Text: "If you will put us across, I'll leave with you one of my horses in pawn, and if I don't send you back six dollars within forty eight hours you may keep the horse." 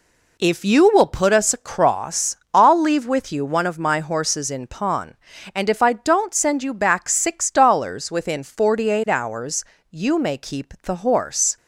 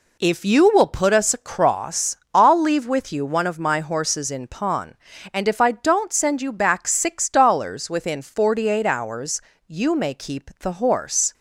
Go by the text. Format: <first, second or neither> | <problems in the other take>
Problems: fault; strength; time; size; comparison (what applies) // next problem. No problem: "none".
neither | pauses between "hours" and "you"; slight; the same in both